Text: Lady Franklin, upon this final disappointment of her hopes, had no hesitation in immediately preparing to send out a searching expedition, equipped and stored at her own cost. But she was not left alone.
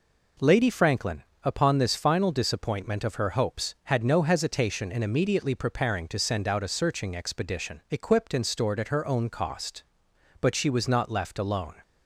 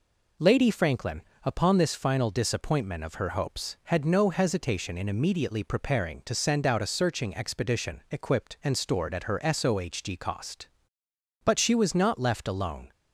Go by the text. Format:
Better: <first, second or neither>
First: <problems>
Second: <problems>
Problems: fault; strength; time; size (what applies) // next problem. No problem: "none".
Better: first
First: none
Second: says "sohg" for "own"; at 9.3 s